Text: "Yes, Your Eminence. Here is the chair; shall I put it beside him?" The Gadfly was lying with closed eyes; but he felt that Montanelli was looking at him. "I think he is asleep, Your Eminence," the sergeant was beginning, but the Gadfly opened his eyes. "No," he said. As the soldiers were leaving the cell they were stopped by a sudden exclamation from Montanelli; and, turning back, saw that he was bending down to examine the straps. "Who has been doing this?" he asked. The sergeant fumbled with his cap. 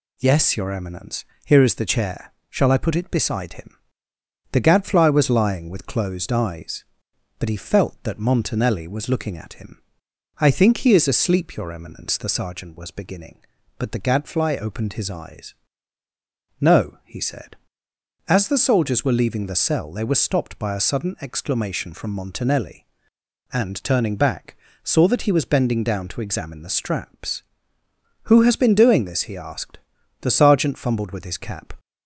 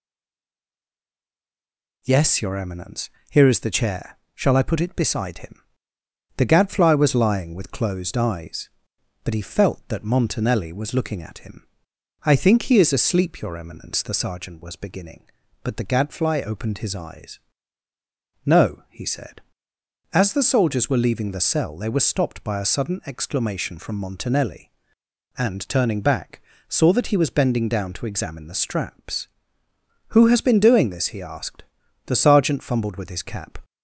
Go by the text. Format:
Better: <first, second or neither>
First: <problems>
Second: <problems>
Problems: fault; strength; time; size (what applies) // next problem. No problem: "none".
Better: first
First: none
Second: stays silent before the first word; noticeable; until 2.0 s; 2.0 s long